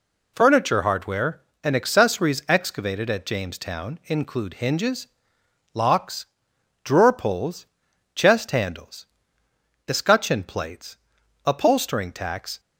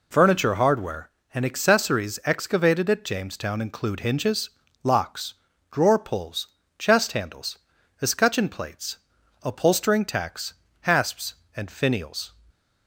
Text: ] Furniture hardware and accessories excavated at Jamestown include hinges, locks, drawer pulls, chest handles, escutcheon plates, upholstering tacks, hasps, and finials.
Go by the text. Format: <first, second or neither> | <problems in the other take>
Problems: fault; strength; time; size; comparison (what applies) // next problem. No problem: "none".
second | stops before "hasps and finials"; at 12.5 s